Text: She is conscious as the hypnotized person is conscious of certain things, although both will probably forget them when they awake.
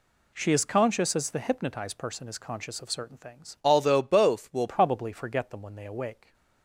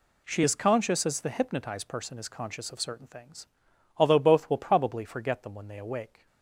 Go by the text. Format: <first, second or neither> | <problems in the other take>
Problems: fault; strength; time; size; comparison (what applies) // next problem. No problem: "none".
second | changes voice from "although" to "will"; from 3.6 to 4.6 s; 1.0 s long